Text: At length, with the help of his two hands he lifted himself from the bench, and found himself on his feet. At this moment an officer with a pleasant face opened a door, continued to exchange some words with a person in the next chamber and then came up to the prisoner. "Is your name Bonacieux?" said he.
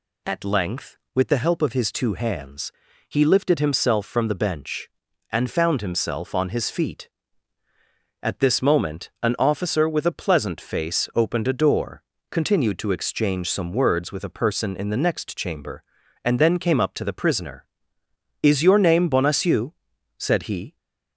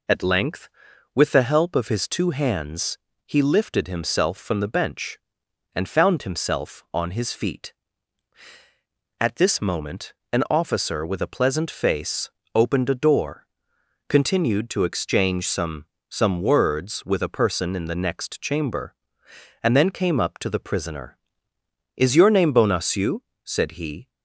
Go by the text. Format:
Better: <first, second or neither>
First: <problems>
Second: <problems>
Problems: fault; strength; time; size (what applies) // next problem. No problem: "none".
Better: first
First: pauses between "hands" and "he"; at 2.7 s; 0.38 s long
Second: pauses between "hands" and "he"; slight; at 2.9 s; 0.28 s long // pauses between "moment" and "an"; slight; at 10.1 s; 0.20 s long // pauses between "face" and "opened"; slight; at 12.2 s; 0.24 s long // says "some" twice; at 16.0 s